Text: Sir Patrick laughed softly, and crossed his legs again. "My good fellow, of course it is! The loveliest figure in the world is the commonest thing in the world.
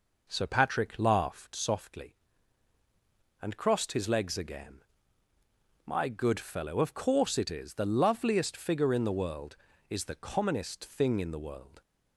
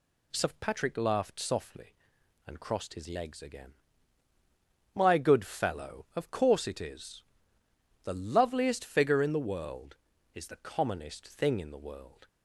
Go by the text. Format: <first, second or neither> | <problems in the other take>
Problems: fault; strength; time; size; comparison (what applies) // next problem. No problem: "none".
second | starts louder than the rest; noticeable; until 1.8 s; 5 dB